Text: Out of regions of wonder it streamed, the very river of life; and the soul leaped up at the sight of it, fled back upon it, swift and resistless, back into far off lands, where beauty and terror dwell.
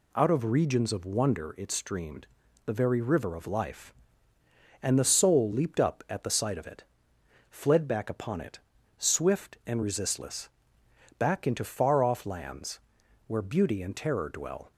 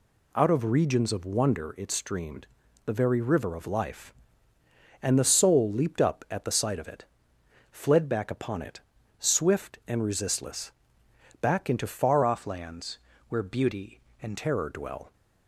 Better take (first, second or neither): first